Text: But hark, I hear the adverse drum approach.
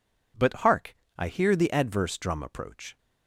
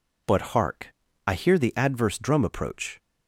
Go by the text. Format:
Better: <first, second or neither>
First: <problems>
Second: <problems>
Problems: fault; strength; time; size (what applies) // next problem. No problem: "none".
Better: neither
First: none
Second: none